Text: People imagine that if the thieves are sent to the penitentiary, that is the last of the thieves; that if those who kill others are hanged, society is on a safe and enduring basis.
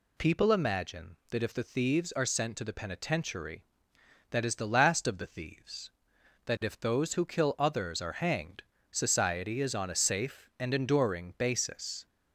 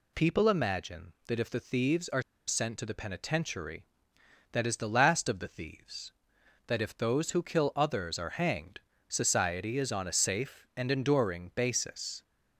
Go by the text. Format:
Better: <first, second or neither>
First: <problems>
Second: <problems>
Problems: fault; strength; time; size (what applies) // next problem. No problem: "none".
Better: first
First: none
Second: pauses between "are" and "sent"; slight; at 2.2 s; 0.25 s long